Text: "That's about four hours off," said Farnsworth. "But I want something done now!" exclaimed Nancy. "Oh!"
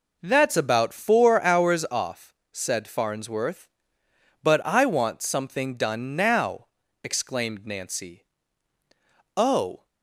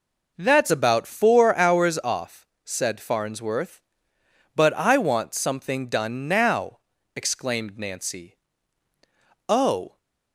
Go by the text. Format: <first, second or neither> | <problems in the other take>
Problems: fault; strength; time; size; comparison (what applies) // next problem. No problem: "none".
neither | none